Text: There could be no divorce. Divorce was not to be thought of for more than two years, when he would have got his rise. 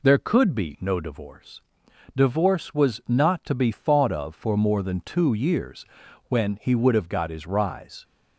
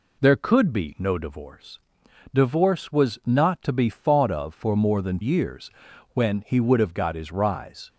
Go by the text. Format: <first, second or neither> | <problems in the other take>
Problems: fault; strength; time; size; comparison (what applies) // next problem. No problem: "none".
first | skips "two"; at 5.2 s